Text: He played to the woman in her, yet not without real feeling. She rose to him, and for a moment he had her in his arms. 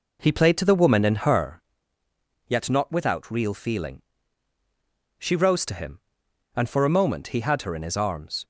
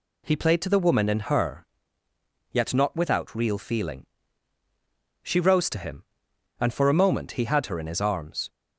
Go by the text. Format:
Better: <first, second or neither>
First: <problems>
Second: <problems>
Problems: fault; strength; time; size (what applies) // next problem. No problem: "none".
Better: second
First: starts louder than the rest; noticeable; until 1.5 s; 4 dB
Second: none